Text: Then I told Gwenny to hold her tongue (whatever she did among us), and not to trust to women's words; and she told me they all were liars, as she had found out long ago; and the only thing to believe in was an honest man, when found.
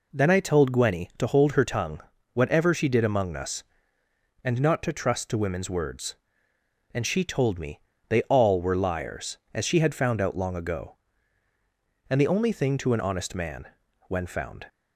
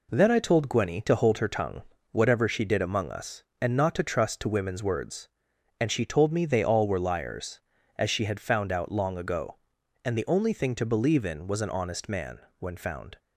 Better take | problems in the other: second | pauses between "me" and "they"; slight; at 7.7 s; 0.30 s long // skips "believe in was"; at 12.9 s

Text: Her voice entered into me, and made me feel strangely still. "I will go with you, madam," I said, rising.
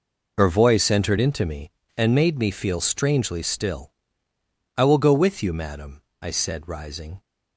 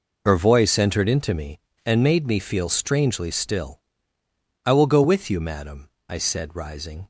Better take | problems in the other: neither | none

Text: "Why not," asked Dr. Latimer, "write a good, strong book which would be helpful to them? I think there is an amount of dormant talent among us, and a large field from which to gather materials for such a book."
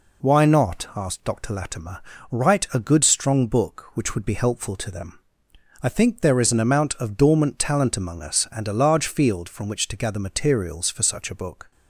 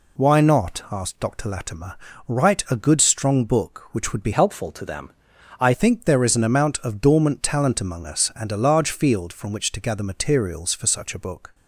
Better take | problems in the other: first | changes voice from "helpful" to "I"; from 4.3 to 5.7 s; 1.4 s long

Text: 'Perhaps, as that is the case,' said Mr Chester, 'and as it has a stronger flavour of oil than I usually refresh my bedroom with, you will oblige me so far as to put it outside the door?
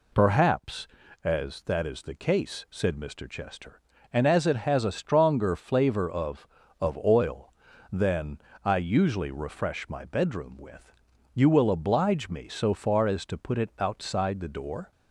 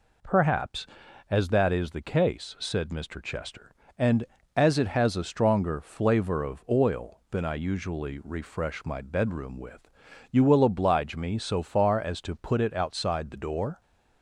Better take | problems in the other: second | says "of" twice; at 6.7 s // pauses between "than" and "I"; slight; at 8.3 s; 0.26 s long

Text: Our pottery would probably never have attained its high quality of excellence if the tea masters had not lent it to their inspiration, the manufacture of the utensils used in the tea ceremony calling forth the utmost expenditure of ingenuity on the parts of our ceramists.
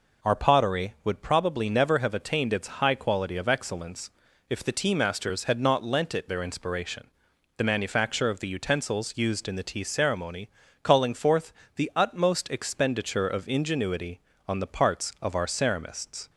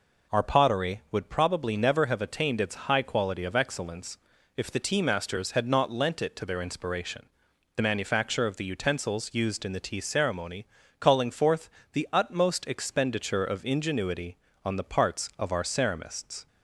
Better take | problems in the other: second | pauses between "excellence" and "if"; at 4.1 s; 0.38 s long; also in the second // skips "to"; at 6.2 s // pauses between "ceremony" and "calling"; slight; at 10.4 s; 0.32 s long; slight in the second // pauses between "forth" and "the"; slight; at 11.5 s; 0.24 s long; slight in the second

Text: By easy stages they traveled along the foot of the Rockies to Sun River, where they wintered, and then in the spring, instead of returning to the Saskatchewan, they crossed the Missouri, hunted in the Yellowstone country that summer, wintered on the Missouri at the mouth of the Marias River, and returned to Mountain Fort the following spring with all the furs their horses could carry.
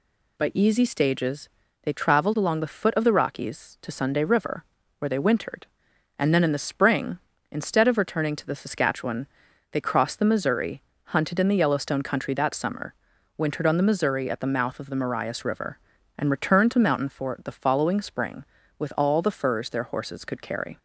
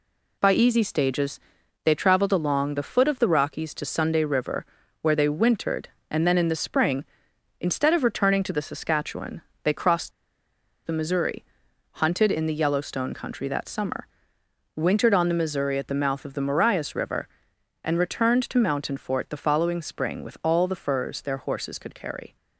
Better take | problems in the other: first | pauses between "stages" and "they"; at 1.3 s; 0.44 s long; slight in the first // pauses between "crossed" and "the"; noticeable; at 10.1 s; 0.75 s long

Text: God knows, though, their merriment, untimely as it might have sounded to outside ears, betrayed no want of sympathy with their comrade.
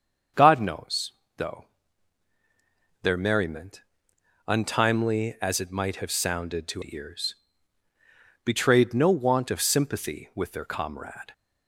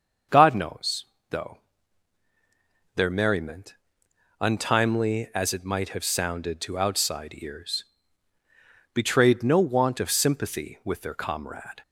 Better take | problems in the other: second | starts louder than the rest; until 1.5 s; 6.5 dB; also in the second // skips "outside"; at 6.8 s

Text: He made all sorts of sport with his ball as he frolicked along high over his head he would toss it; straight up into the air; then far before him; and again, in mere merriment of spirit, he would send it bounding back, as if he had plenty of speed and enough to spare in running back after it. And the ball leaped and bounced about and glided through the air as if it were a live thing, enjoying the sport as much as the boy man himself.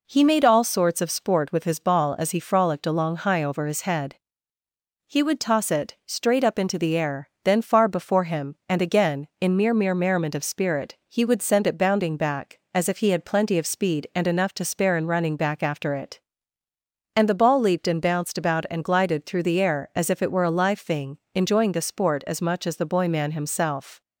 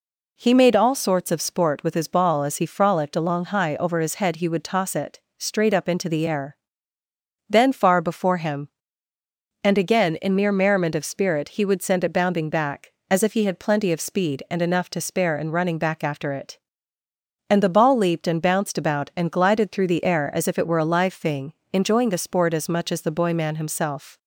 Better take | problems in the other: second | pauses between "head" and "he"; noticeable; at 4.1 s; 0.92 s long // says "mere" twice; at 9.7 s

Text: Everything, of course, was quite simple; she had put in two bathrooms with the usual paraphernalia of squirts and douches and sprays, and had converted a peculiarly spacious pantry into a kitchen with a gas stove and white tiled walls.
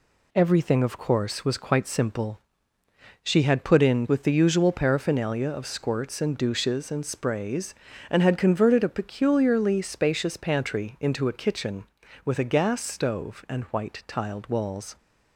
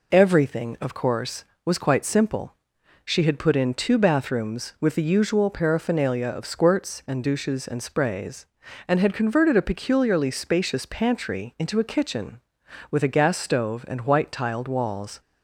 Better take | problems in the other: second | skips "two bathrooms"; at 4.0 s

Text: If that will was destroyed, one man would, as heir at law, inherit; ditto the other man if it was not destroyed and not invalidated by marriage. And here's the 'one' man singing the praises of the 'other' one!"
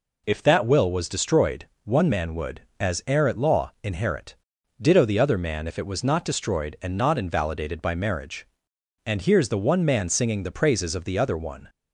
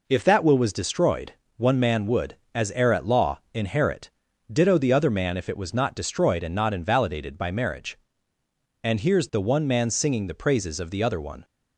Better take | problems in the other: neither | none

